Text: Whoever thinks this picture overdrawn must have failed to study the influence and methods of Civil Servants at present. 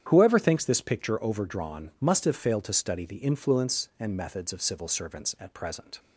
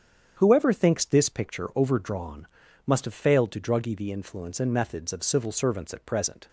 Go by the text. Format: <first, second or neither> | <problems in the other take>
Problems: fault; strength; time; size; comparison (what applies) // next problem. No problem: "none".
first | starts louder than the rest; strong; until 1.3 s; 8.5 dB; strong in the first // pauses between "overdrawn" and "must"; at 2.4 s; 0.40 s long // says "druggy" for "study"; at 3.5 s